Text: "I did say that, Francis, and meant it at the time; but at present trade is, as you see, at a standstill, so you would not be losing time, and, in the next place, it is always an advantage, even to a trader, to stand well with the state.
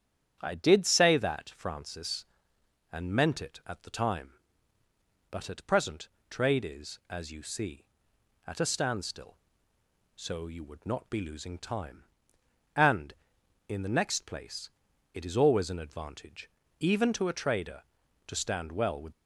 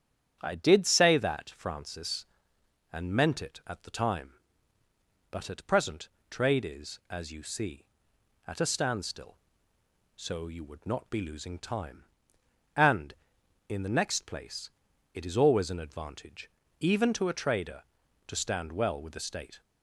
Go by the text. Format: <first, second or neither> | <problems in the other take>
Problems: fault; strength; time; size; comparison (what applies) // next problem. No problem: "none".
second | starts louder than the rest; strong; until 1.4 s; 9.5 dB; strong in the second // pauses between "present" and "trade"; slight; at 6.0 s; 0.22 s long; slight in the second // stops before "the state"; at 19.1 s